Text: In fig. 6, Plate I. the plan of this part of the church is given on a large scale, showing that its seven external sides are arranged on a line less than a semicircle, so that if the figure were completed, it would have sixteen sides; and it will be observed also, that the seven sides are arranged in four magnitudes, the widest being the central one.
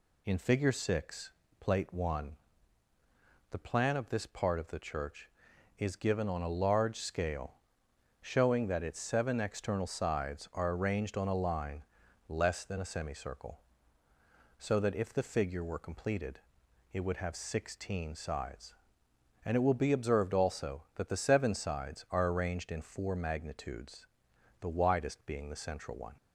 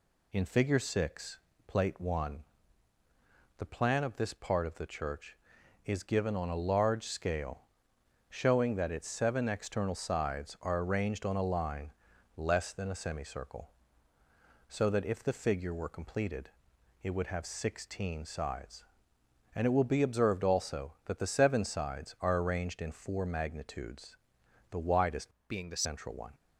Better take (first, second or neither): first